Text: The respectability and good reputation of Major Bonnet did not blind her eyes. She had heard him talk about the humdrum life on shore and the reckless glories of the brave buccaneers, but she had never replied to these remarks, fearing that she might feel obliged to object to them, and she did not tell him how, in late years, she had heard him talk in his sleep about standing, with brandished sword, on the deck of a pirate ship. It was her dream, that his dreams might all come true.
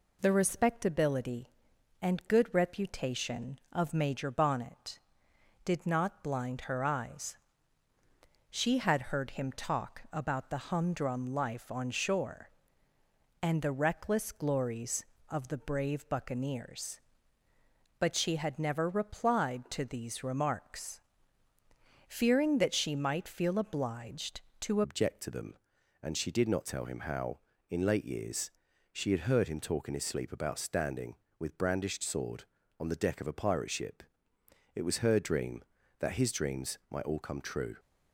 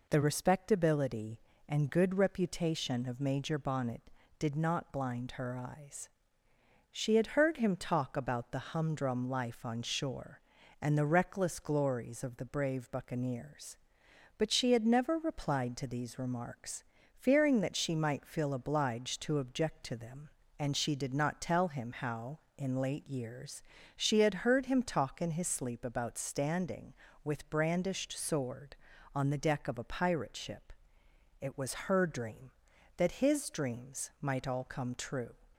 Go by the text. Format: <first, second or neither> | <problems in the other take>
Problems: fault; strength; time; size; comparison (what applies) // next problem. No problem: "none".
second | changes voice at "object"; from 24.8 s on; 12.9 s long